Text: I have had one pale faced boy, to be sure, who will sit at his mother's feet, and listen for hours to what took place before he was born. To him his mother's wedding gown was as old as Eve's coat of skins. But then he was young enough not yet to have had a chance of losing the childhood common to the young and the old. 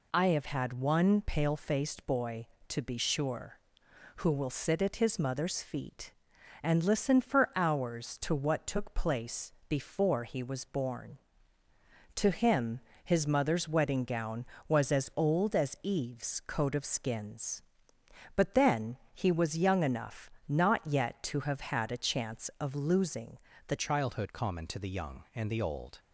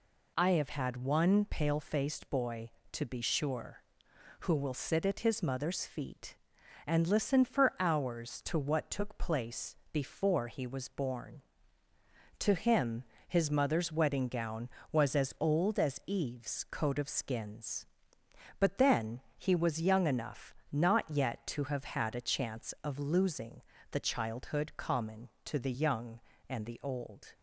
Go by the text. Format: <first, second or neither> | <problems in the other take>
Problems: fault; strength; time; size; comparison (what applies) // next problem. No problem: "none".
second | pauses between "place" and "before"; slight; at 9.5 s; 0.16 s long; slight in the second // pauses between "him" and "his"; slight; at 12.8 s; 0.24 s long; slight in the second // pauses between "then" and "he"; slight; at 18.9 s; 0.16 s long; slight in the second // pauses between "enough" and "not"; slight; at 20.3 s; 0.20 s long; slight in the second // pauses between "losing" and "the"; slight; at 23.3 s; 0.30 s long; slight in the second // changes voice at "childhood"; from 23.7 s on; 2.2 s long